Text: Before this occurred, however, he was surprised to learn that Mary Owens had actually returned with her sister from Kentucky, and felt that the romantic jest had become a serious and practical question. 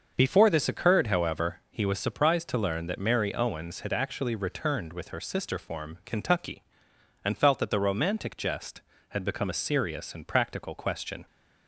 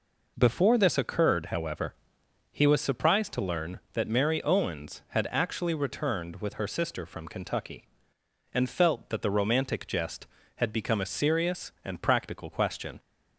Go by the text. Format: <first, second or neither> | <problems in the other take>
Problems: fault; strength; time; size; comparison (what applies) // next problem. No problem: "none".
second | starts louder than the rest; until 1.1 s; 6.5 dB // says "form" for "from"; at 5.5 s